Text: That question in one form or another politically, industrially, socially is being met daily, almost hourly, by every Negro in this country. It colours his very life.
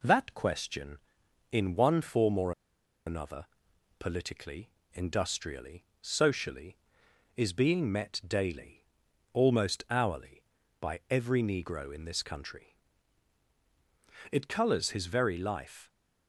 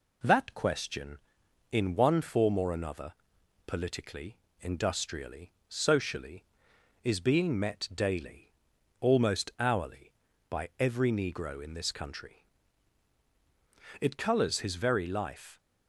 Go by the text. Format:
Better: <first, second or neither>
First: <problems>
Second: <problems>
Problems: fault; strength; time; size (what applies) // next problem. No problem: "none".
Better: second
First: pauses between "or" and "another"; noticeable; at 2.5 s; 0.54 s long // pauses between "another" and "politically"; noticeable; at 3.4 s; 0.56 s long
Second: pauses between "another" and "politically"; noticeable; at 3.1 s; 0.56 s long